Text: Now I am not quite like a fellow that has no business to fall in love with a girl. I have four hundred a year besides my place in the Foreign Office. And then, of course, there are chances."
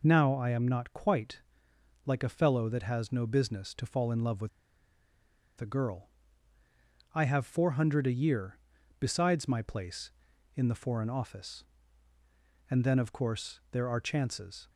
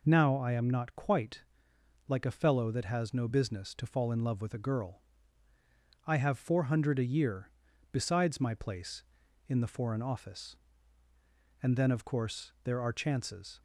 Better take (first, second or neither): second